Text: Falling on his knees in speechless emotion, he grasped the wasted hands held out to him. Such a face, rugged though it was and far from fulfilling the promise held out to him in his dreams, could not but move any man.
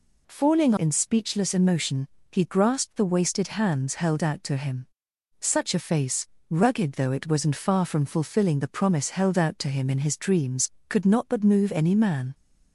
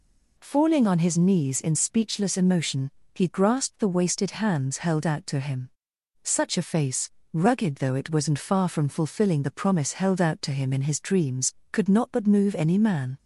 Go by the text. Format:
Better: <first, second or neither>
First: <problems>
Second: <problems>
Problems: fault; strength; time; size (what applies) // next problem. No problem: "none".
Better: second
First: skips "on his knees"; at 0.7 s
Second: none